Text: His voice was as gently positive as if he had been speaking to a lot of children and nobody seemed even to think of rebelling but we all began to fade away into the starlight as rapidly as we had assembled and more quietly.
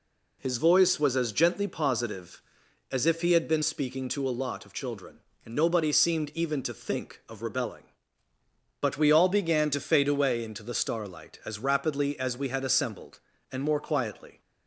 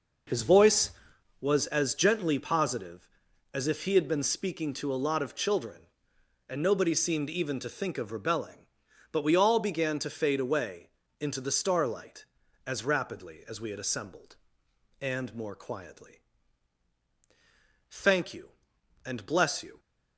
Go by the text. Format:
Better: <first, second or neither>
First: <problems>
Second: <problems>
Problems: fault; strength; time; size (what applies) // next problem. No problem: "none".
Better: first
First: none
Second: pauses between "away" and "into"; slight; at 10.8 s; 0.32 s long // goes on to say "Thank you and bless you"; strong; from 17.8 s on; 1.9 s long